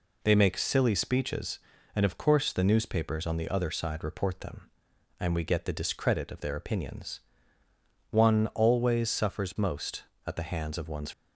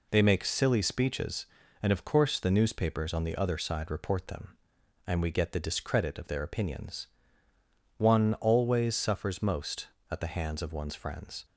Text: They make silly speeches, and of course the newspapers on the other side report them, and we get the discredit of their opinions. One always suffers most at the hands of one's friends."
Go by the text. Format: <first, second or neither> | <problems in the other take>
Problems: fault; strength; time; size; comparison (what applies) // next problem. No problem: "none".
second | stops before "friends"; at 11.1 s